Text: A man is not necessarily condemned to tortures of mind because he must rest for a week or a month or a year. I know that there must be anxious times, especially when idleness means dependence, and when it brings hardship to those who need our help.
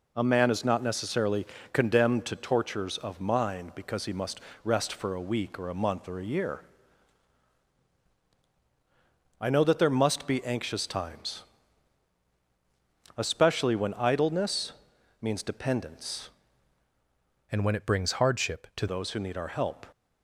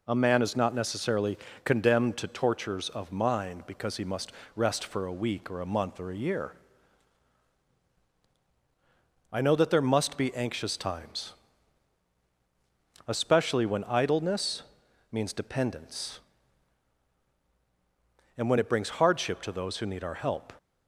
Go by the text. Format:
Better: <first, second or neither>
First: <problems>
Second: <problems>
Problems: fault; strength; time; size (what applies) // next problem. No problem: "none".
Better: second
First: pauses between "necessarily" and "condemned"; slight; at 1.4 s; 0.24 s long // pauses between "must" and "rest"; slight; at 4.4 s; 0.24 s long // pauses between "idleness" and "means"; noticeable; at 14.7 s; 0.48 s long // changes voice from "and" to "to"; from 17.5 to 18.8 s; 1.3 s long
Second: pauses between "necessarily" and "condemned"; slight; at 1.3 s; 0.24 s long // pauses between "must" and "rest"; slight; at 4.3 s; 0.24 s long // pauses between "idleness" and "means"; noticeable; at 14.6 s; 0.48 s long